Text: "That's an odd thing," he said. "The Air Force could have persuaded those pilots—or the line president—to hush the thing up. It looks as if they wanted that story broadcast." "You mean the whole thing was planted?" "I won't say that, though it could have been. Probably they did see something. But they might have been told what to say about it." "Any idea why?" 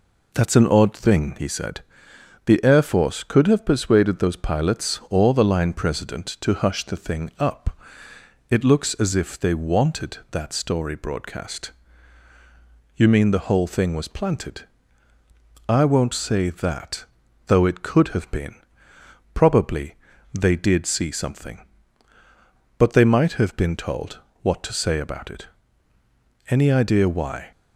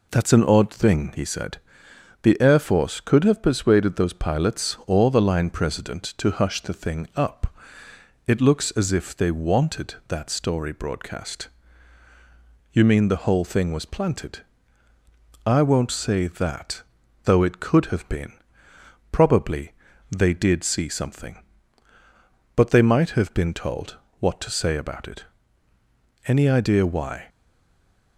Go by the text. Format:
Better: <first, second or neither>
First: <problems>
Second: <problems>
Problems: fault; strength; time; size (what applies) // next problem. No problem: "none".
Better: first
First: pauses between "Probably" and "they"; at 19.9 s; 0.38 s long // pauses between "told" and "what"; slight; at 24.1 s; 0.24 s long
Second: pauses between "Probably" and "they"; at 19.7 s; 0.38 s long // pauses between "told" and "what"; slight; at 23.9 s; 0.24 s long // stays silent after the last word; slight; from 27.2 s on; 0.9 s long